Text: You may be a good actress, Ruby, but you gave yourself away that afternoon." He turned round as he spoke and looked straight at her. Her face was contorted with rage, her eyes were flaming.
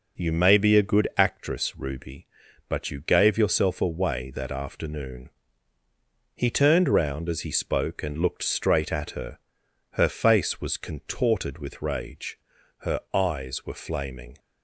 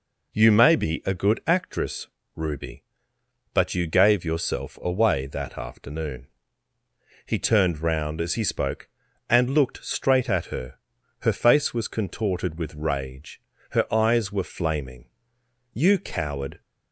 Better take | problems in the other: first | goes on to say "You coward"; noticeable; from 15.7 s on; 0.88 s long

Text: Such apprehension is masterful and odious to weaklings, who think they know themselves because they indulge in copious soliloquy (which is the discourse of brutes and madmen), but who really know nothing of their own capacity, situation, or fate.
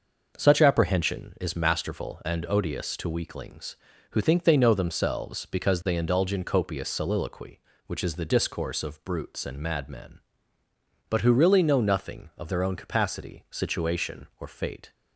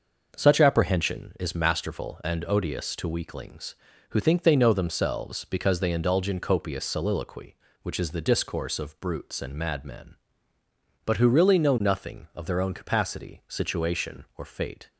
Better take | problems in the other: neither | none

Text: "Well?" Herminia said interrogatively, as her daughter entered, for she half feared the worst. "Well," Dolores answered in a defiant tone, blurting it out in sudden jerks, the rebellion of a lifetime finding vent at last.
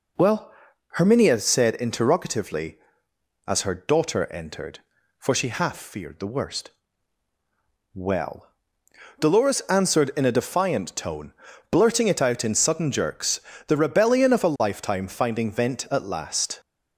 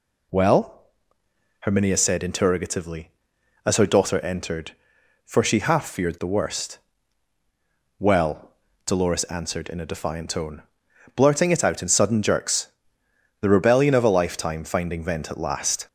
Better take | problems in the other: neither | none

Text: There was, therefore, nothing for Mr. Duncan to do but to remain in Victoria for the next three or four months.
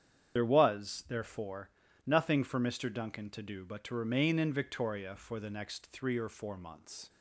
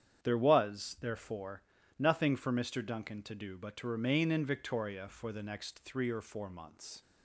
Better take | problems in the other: second | loses the start of "There"; at 0.3 s; 55 ms // starts louder than the rest; strong; until 1.4 s; 8.5 dB; strong in the second

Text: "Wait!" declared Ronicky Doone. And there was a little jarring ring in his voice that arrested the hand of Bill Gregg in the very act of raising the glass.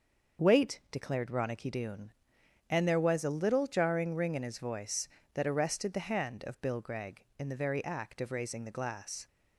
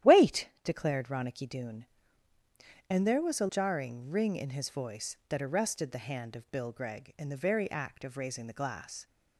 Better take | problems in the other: first | starts louder than the rest; strong; until 1.2 s; 12 dB; also in the first // skips "little"; at 3.4 s

